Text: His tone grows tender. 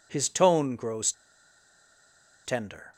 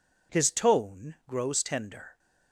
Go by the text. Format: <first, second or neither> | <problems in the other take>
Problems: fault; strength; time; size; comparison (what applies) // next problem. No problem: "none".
second | pauses between "grows" and "tender"; strong; at 1.1 s; 1.3 s long